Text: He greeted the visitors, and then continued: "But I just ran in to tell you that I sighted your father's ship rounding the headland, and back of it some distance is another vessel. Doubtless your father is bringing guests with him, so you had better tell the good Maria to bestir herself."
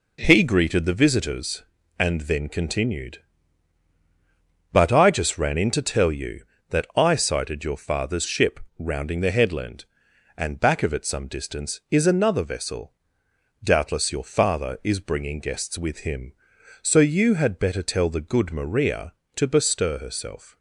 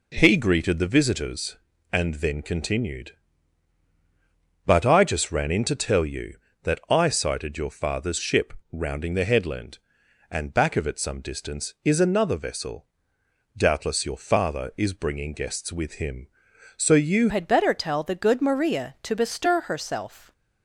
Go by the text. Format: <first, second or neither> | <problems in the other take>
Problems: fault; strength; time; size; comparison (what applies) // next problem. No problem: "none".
first | pauses between "ship" and "rounding"; slight; at 8.5 s; 0.18 s long; slight in the first // changes voice at "had"; from 17.2 s on; 3.1 s long